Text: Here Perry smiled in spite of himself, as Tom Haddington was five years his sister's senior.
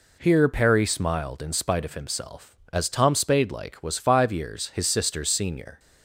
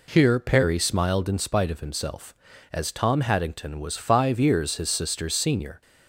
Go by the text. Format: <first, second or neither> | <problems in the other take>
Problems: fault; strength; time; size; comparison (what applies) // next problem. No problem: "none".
second | says "Spadelike" for "Haddington"; at 3.1 s